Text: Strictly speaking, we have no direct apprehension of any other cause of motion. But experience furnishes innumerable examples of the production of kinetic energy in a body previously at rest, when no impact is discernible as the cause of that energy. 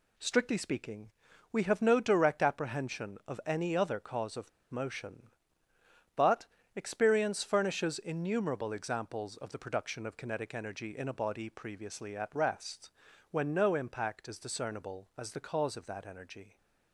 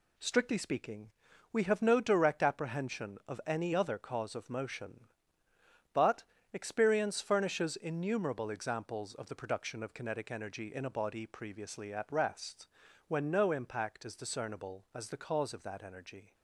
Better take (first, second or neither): second